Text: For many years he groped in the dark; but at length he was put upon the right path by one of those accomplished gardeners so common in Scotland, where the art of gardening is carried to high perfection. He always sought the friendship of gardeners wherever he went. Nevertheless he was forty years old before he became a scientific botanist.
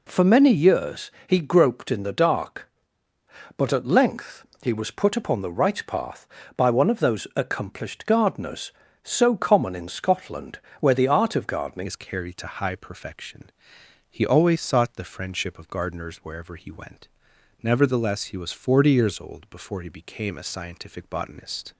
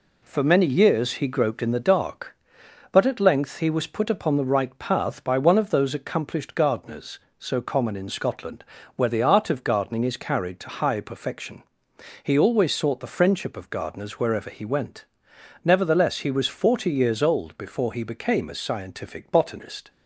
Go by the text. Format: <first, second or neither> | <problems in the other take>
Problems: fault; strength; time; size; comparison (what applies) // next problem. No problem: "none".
second | pauses between "years" and "he"; slight; at 1.1 s; 0.16 s long // pauses between "length" and "he"; slight; at 4.4 s; 0.16 s long // changes voice at "is"; from 11.8 s on; 9.9 s long